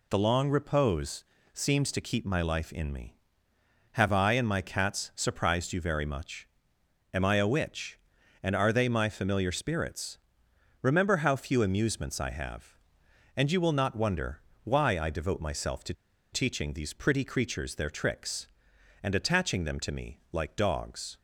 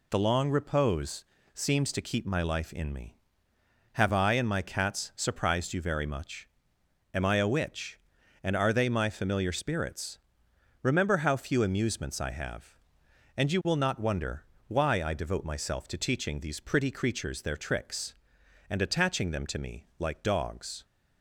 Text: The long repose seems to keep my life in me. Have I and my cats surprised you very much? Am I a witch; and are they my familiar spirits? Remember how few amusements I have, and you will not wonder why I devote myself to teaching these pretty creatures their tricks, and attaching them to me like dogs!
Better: second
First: pauses between "repose" and "seems"; slight; at 1.2 s; 0.30 s long // pauses between "wonder" and "why"; slight; at 14.4 s; 0.22 s long // pauses between "to" and "teaching"; at 15.9 s; 0.37 s long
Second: pauses between "repose" and "seems"; slight; at 1.2 s; 0.30 s long // pauses between "wonder" and "why"; slight; at 14.4 s; 0.22 s long

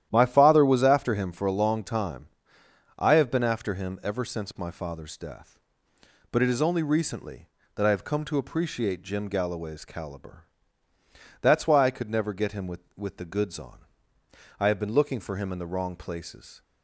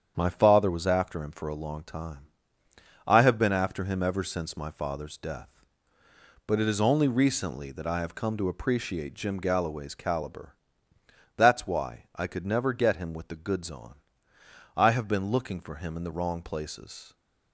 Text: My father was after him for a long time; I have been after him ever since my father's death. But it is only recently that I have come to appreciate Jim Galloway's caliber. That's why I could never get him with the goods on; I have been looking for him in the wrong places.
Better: second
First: starts louder than the rest; strong; until 1.1 s; 11.5 dB // says "with" twice; at 12.9 s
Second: starts louder than the rest; strong; until 1.1 s; 8 dB

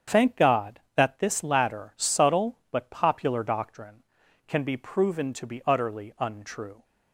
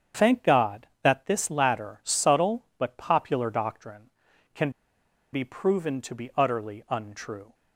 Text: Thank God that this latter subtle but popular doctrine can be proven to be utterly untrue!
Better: first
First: starts louder than the rest; strong; until 1.2 s; 7.5 dB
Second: starts louder than the rest; strong; until 1.3 s; 7.5 dB // pauses between "can" and "be"; noticeable; at 4.6 s; 0.63 s long

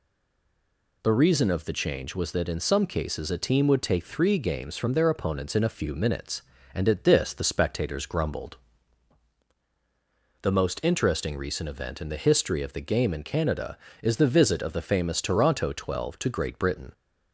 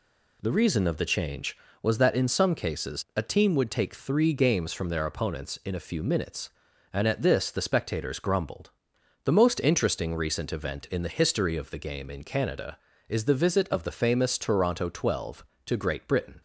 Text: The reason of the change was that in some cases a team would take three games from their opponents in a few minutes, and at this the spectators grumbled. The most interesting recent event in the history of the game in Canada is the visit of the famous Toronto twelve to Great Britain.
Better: second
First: stays silent before the first word; until 1.0 s; 1.0 s long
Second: none

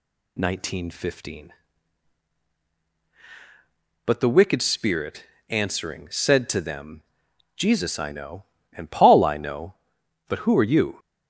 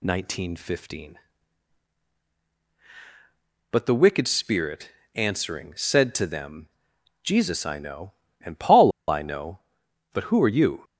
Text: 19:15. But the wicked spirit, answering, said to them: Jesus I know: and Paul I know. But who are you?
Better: first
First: none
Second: pauses between "Paul" and "I"; slight; at 8.9 s; 0.16 s long

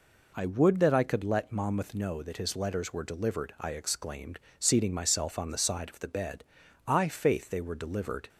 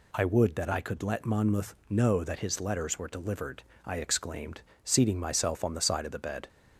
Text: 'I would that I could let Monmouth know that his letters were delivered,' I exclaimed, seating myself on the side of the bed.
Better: second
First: goes on to say "I faith they were delivered"; from 6.8 s on; 1.4 s long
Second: none

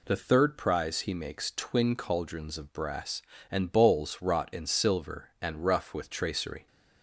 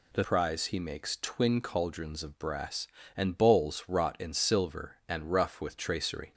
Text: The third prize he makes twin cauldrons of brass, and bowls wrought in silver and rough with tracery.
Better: first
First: none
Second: skips "third"; at 0.2 s

